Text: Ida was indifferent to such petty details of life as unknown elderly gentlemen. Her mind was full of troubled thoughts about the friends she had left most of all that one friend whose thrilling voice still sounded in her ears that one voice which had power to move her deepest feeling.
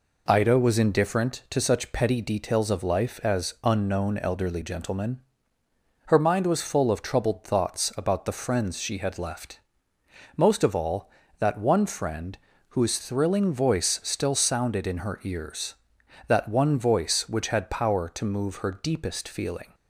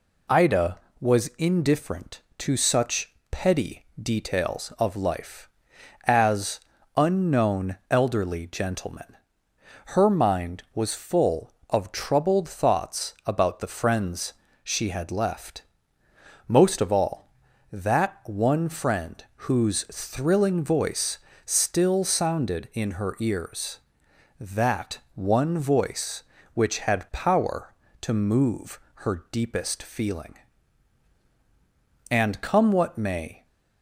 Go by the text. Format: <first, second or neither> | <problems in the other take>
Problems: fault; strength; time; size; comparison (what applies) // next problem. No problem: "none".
first | pauses between "such" and "petty"; slight; at 3.1 s; 0.18 s long // pauses between "petty" and "details"; slight; at 3.8 s; 0.16 s long // pauses between "as" and "unknown"; slight; at 6.5 s; 0.36 s long // pauses between "friends" and "she"; slight; at 14.3 s; 0.30 s long // pauses between "left" and "most"; noticeable; at 15.6 s; 0.84 s long; noticeable in the first // pauses between "friend" and "whose"; slight; at 19.2 s; 0.24 s long; slight in the first // pauses between "voice" and "still"; slight; at 21.1 s; 0.26 s long // pauses between "that" and "one"; slight; at 24.9 s; 0.16 s long // pauses between "move" and "her"; slight; at 28.7 s; 0.22 s long // goes on to say "And come what may"; from 32.0 s on; 1.3 s long